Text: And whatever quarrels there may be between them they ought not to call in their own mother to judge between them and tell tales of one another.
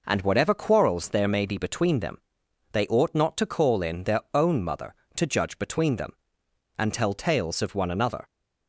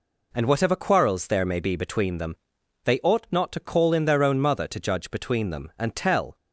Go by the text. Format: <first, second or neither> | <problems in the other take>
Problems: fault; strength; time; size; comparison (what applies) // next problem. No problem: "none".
first | pauses between "them" and "they"; noticeable; at 2.3 s; 0.48 s long; noticeable in the first // stops before "tales of one another"; at 6.3 s